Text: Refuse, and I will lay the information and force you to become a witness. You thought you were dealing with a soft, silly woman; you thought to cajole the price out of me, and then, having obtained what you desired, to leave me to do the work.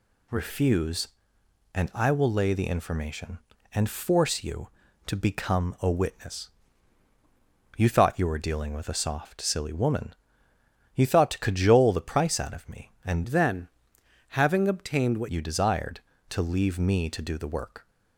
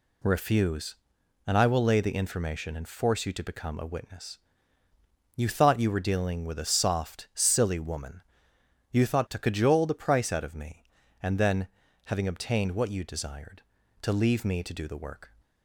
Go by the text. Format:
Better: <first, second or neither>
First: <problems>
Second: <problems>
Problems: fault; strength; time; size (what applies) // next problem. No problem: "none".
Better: second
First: changes voice from "then" to "what"; from 13.2 to 15.2 s; 2.0 s long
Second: none